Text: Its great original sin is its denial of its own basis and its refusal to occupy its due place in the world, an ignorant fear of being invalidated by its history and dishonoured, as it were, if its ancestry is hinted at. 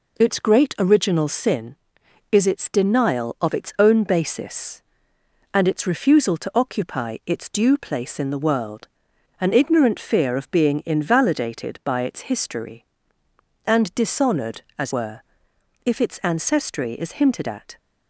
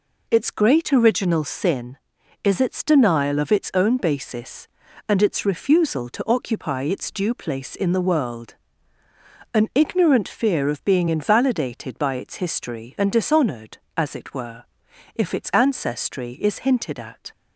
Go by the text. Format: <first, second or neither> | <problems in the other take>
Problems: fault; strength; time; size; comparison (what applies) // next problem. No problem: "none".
second | skips "it"; at 14.9 s